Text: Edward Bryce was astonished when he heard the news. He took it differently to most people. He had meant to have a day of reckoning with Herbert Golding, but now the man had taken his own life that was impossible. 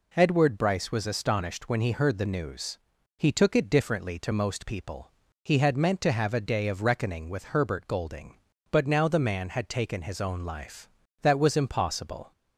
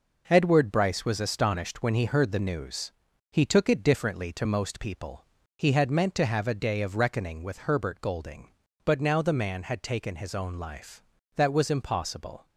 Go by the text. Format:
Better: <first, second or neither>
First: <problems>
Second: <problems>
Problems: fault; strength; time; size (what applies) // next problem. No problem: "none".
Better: first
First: none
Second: gets quieter; throughout; 6.5 dB